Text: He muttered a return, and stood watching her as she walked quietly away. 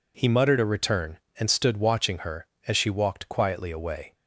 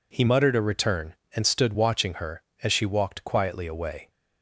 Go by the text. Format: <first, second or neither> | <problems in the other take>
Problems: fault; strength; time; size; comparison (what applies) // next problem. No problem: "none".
neither | none